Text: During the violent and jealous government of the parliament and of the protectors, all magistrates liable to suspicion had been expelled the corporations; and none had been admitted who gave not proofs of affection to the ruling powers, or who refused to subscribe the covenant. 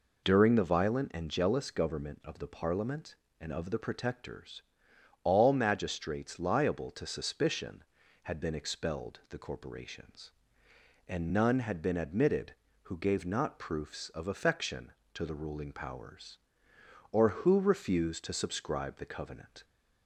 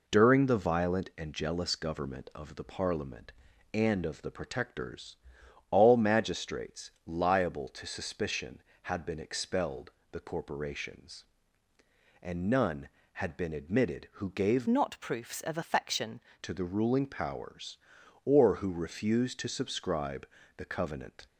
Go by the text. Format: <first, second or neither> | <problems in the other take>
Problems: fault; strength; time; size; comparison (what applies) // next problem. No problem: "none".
first | pauses between "expelled" and "the"; slight; at 9.9 s; 0.22 s long // changes voice from "not" to "affection"; from 14.6 to 16.1 s; 1.5 s long // pauses between "subscribe" and "the"; slight; at 20.2 s; 0.30 s long